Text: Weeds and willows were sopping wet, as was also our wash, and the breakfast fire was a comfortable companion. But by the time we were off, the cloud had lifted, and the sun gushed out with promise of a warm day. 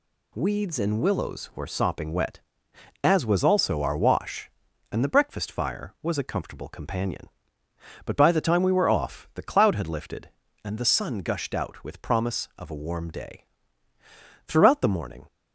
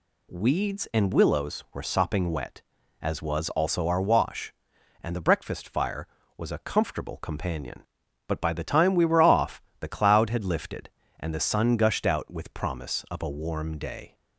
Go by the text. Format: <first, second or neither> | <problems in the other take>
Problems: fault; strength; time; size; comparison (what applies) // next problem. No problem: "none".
second | goes on to say "Throughout the morning"; noticeable; from 14.4 s on; 0.80 s long